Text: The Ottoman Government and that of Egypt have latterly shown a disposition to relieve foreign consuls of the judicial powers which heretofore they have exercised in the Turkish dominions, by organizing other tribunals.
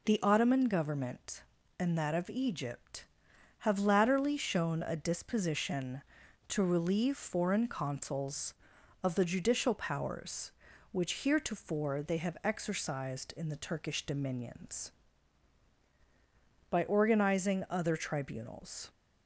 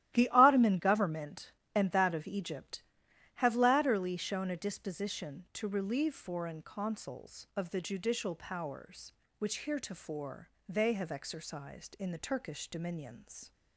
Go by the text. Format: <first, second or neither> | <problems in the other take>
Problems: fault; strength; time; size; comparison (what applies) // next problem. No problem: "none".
first | starts louder than the rest; strong; until 1.1 s; 13.5 dB // pauses between "heretofore" and "they"; slight; at 10.4 s; 0.20 s long // stops before "by organizing other tribunals"; at 13.5 s